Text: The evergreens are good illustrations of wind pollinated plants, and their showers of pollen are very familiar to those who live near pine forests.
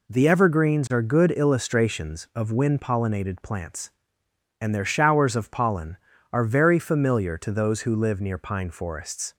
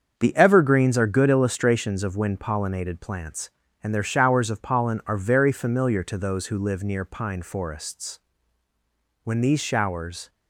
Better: first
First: none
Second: starts louder than the rest; until 1.1 s; 7 dB // goes on to say "When these showers"; noticeable; from 9.2 s on; 1.0 s long

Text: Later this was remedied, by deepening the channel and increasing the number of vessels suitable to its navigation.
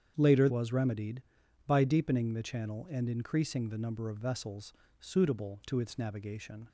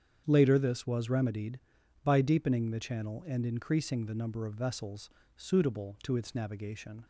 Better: second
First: starts louder than the rest; strong; until 1.1 s; 8 dB // skips "this"; at 0.4 s // pauses between "vessels" and "suitable"; slight; at 4.7 s; 0.26 s long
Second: starts louder than the rest; strong; until 1.2 s; 8 dB // pauses between "vessels" and "suitable"; slight; at 5.0 s; 0.26 s long

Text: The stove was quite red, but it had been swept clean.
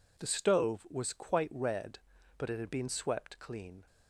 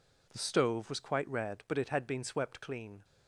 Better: neither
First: none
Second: none

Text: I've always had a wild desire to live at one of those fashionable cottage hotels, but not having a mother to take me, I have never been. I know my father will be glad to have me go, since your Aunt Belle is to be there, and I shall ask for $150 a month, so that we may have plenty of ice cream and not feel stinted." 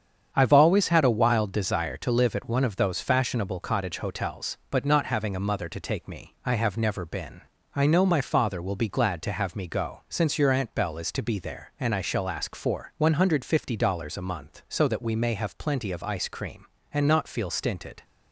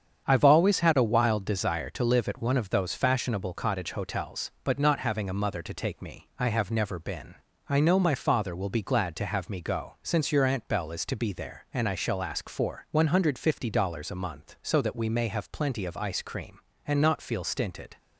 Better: neither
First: starts louder than the rest; strong; until 1.3 s; 8 dB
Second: starts louder than the rest; strong; until 1.2 s; 8 dB

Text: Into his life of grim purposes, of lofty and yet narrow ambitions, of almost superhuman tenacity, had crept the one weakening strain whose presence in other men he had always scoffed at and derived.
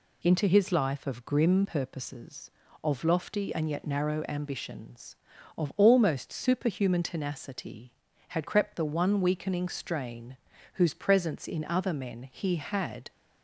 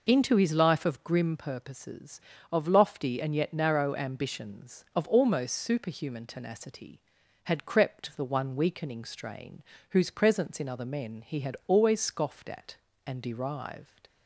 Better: second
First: pauses between "strain" and "whose"; at 10.3 s; 0.38 s long // stops before "always scoffed at and derived"; at 13.1 s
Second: pauses between "strain" and "whose"; slight; at 9.6 s; 0.28 s long

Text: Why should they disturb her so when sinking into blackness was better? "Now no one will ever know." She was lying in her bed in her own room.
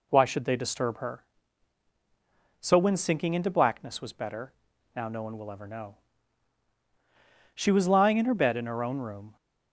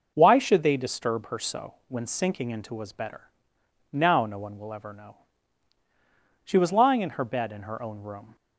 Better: first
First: none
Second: skips "blackness"; at 2.7 s

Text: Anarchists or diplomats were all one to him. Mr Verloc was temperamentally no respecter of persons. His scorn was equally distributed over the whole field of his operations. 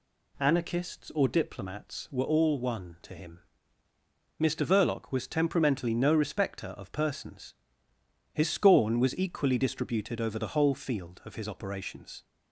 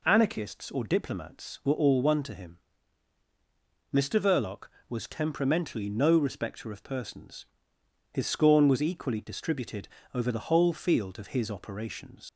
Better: first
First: none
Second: pauses between "distributed" and "over"; slight; at 9.8 s; 0.26 s long // leaves "operations" unfinished; at 12.2 s; 85 ms

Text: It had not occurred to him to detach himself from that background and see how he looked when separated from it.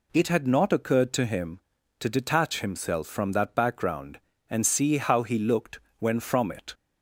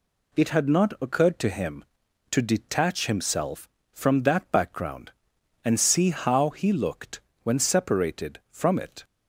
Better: second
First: pauses between "looked" and "when"; slight; at 5.7 s; 0.22 s long // skips "separated"; at 6.1 s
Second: pauses between "looked" and "when"; slight; at 7.1 s; 0.24 s long

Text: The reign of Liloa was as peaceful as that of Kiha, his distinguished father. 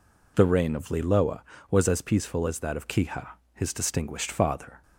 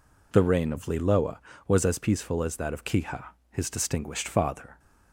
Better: neither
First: none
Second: none

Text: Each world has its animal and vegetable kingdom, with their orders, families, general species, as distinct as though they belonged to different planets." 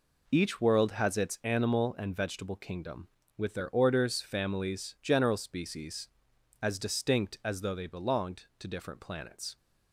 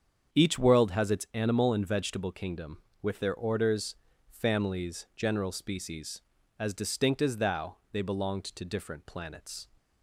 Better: first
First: none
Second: starts louder than the rest; strong; until 1.3 s; 7.5 dB // says "thou" for "though"; at 7.3 s

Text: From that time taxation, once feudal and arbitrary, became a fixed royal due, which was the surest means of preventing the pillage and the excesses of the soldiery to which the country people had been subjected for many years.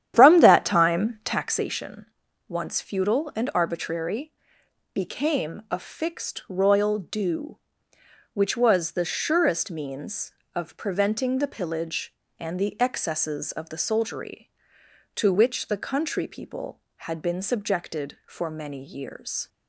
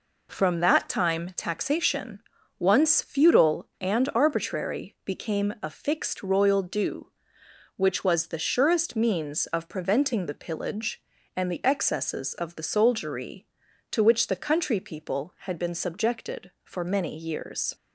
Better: second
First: starts louder than the rest; strong; until 1.7 s; 10.5 dB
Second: none

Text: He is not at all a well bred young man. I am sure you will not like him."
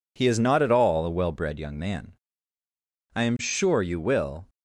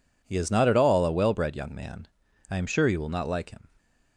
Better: second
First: stops before "not like him"; at 4.4 s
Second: none

